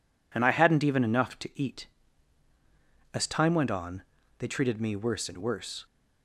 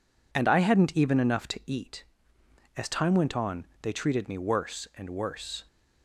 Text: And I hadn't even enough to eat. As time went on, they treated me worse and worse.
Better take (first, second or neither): neither